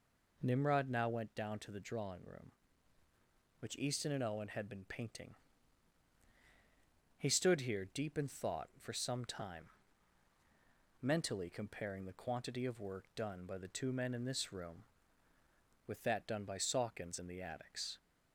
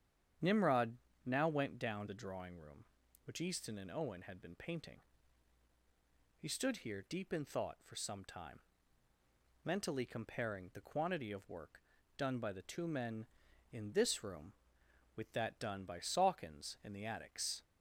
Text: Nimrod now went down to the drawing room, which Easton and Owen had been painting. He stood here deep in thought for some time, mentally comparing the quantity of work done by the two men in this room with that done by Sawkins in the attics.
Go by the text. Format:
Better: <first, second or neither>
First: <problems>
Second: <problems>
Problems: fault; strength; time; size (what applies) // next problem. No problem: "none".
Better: first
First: none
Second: starts louder than the rest; strong; until 1.6 s; 9 dB // pauses between "Nimrod" and "now"; slight; at 0.9 s; 0.28 s long // skips "to"; at 2.0 s // pauses between "work" and "done"; slight; at 11.8 s; 0.36 s long